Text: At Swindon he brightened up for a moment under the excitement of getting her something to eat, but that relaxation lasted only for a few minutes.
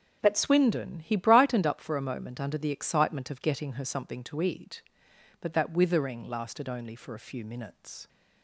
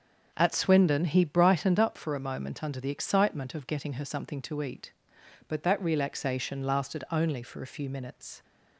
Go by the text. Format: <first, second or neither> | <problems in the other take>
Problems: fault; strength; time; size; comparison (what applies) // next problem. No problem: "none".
second | starts louder than the rest; until 1.2 s; 6.5 dB; also in the second // says "withering" for "relaxation"; at 5.7 s